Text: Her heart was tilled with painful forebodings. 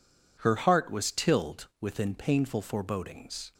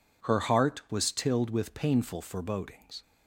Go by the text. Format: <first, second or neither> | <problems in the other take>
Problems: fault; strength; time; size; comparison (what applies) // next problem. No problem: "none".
second | says "within" for "with"; at 1.8 s